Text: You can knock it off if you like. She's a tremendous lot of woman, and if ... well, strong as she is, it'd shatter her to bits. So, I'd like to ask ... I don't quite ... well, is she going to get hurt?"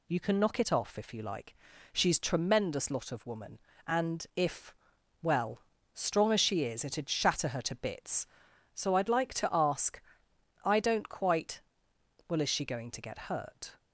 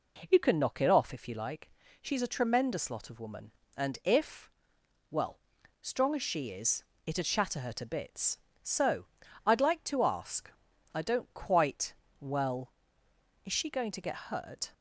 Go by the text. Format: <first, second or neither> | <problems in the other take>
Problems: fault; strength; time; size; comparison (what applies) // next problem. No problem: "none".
second | skips "a"; at 2.1 s